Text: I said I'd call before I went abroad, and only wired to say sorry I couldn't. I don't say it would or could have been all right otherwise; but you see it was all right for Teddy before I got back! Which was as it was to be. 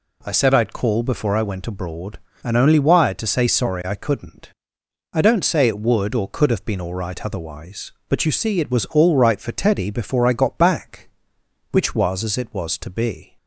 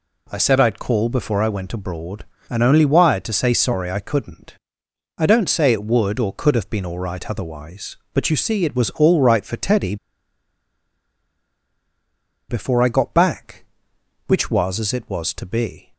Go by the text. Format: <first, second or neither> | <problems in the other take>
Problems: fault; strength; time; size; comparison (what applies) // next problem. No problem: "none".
first | pauses between "Teddy" and "before"; strong; at 9.9 s; 2.5 s long